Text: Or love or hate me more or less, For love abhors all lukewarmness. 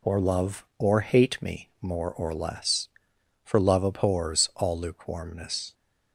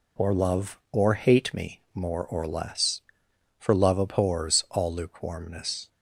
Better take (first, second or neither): neither